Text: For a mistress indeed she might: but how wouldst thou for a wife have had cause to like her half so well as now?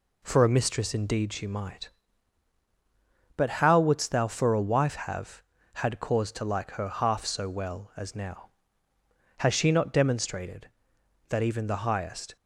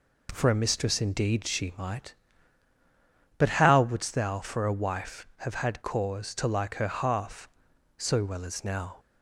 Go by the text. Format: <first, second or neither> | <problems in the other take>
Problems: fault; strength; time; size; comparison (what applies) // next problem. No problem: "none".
second | goes on to say "Has she not demonstrated that even the highest"; strong; from 9.3 s on; 2.9 s long